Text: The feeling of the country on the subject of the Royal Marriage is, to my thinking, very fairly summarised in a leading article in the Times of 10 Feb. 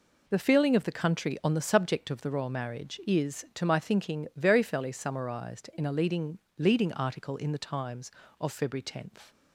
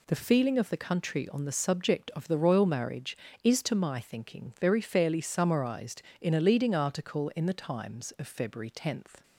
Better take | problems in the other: second | says "leading" twice; at 6.5 s

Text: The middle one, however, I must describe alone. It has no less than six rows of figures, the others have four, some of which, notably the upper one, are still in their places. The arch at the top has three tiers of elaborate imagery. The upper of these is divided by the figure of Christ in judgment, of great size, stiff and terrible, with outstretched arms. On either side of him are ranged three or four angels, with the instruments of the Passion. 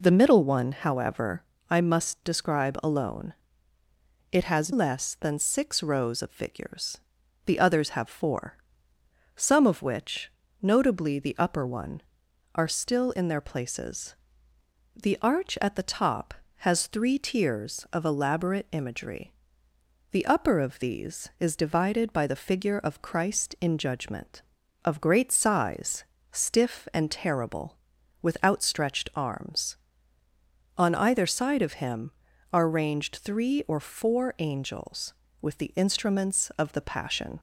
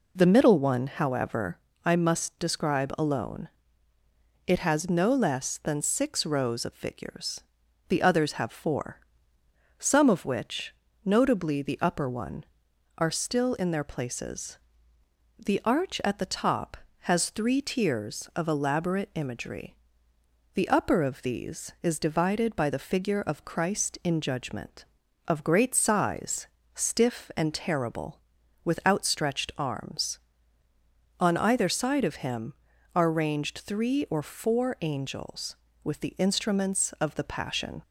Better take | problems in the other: second | skips "no"; at 4.7 s

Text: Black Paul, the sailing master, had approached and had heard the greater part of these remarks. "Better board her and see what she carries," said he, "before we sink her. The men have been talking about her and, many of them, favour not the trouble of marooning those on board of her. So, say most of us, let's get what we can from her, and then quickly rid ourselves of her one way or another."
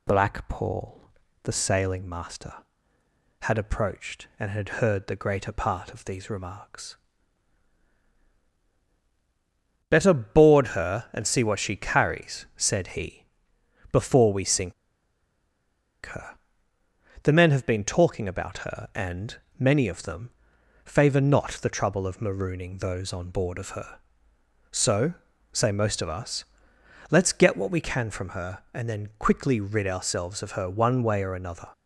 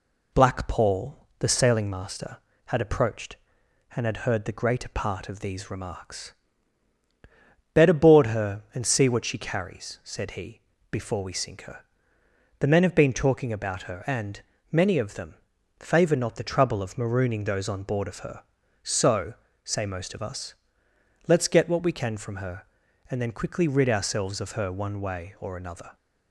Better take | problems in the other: second | pauses between "sink" and "her"; strong; at 14.7 s; 1.3 s long

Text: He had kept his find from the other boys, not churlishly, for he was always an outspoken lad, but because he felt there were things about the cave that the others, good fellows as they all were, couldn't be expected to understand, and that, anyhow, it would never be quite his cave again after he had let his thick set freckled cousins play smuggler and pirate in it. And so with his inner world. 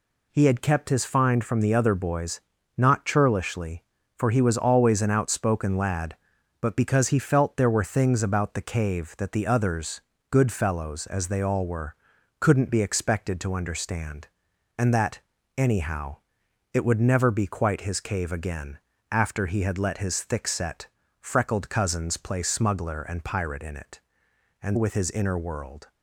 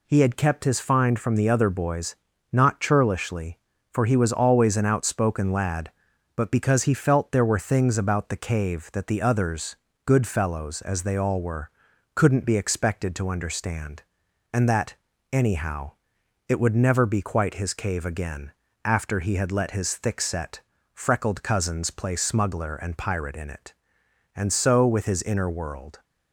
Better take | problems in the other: second | pauses between "again" and "after"; slight; at 18.7 s; 0.34 s long; slight in the second // pauses between "set" and "freckled"; slight; at 20.8 s; 0.34 s long; slight in the second // skips "so"; at 24.7 s

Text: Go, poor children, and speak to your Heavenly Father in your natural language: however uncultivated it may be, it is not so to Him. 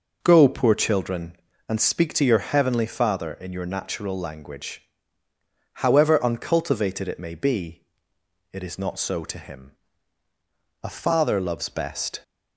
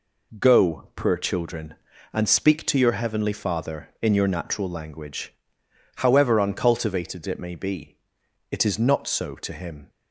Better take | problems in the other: second | goes on to say "A father loves best"; from 10.8 s on; 1.4 s long

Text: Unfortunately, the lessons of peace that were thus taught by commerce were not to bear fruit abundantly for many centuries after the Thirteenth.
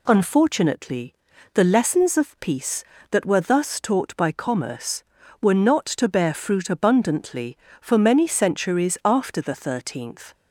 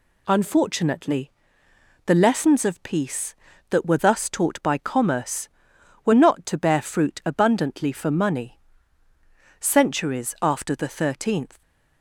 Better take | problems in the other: first | says "money" for "many"; at 8.1 s

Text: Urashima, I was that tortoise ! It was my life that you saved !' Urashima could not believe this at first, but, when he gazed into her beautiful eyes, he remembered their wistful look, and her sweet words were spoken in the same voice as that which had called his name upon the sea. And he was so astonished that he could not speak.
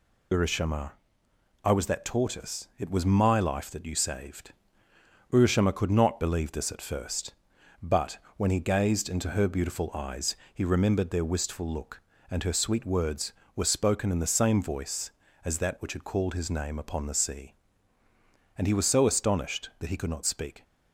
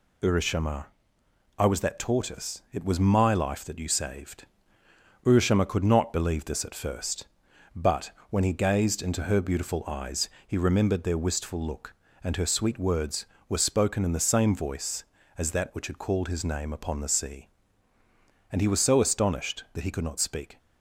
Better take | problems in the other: second | loses the start of "Urashima"; at 0.3 s; 35 ms

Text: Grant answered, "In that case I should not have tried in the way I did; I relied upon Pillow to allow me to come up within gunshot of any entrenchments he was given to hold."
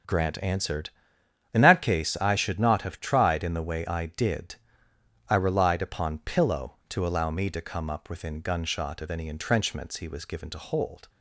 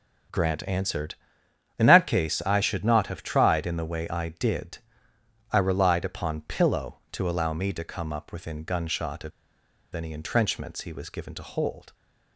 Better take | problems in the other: first | starts louder than the rest; strong; until 1.9 s; 7.5 dB; strong in the first // pauses between "of" and "any"; noticeable; at 9.3 s; 0.64 s long

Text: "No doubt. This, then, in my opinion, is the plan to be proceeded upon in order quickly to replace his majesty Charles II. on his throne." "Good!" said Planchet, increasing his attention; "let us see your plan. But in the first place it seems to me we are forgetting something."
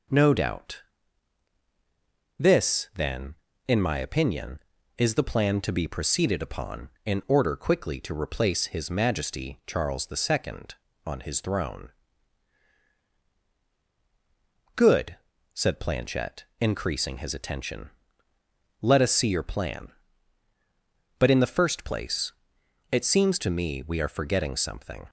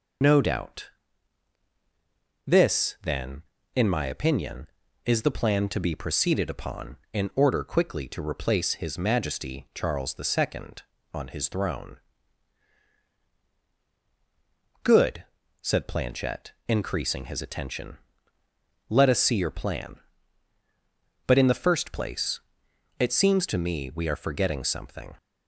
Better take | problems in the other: first | loses the start of "No"; at 0.2 s; 30 ms // pauses between "place" and "it"; noticeable; at 22.4 s; 0.58 s long; noticeable in the first

